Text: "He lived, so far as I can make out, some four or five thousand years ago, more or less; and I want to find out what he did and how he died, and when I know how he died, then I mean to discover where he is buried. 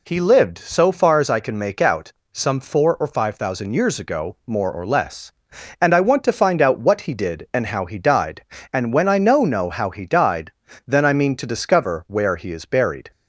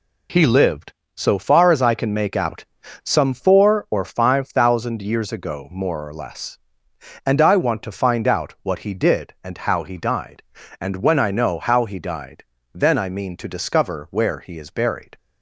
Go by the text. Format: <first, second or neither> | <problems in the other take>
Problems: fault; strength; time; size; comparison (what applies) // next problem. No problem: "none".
second | says "know" twice; at 9.4 s